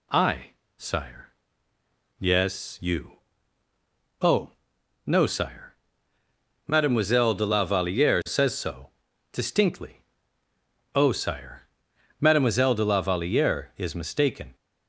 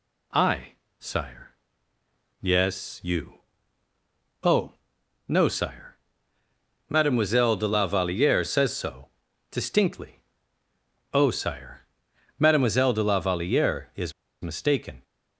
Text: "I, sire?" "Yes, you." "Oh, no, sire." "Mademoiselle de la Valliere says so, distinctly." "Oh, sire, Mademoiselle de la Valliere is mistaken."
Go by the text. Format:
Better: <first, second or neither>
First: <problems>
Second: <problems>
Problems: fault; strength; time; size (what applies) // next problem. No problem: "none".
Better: first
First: none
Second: pauses between "is" and "mistaken"; slight; at 14.1 s; 0.30 s long